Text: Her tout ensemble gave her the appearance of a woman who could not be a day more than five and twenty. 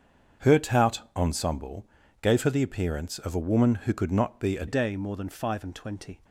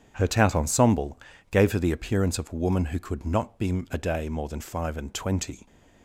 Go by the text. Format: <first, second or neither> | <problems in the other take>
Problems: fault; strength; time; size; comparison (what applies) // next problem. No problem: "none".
second | starts louder than the rest; strong; until 1.5 s; 7.5 dB; strong in the second // pauses between "ensemble" and "gave"; slight; at 1.8 s; 0.34 s long; slight in the second // changes voice at "day"; from 4.6 s on; 1.5 s long